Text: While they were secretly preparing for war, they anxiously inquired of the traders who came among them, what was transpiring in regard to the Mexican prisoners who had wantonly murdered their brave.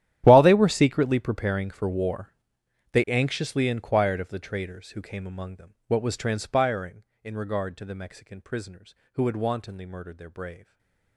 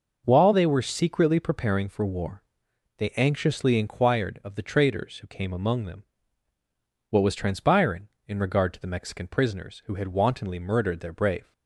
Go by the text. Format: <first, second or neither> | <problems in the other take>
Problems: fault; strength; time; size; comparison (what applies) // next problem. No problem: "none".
second | gets quieter; strong; throughout; 19.5 dB // stays silent after the last word; slight; from 10.5 s on; 0.6 s long